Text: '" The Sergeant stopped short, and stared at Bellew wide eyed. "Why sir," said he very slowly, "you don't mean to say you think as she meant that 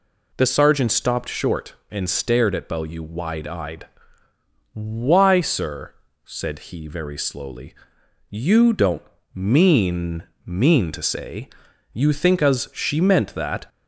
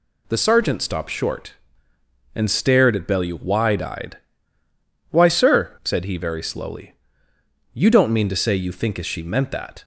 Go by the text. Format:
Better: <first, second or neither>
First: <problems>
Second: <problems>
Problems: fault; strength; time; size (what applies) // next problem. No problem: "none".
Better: second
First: pauses between "don't" and "mean"; slight; at 9.0 s; 0.32 s long // says "mean" twice; at 10.4 s // pauses between "say" and "you"; at 11.5 s; 0.42 s long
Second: none